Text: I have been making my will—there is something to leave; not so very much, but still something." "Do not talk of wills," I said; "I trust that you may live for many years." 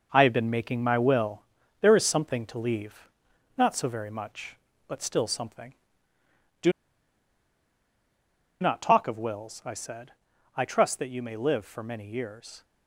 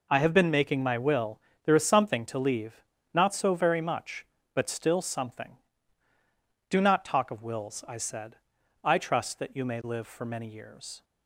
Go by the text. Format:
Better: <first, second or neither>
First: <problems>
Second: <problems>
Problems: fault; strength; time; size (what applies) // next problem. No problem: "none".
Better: second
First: pauses between "Do" and "not"; strong; at 6.7 s; 1.8 s long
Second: none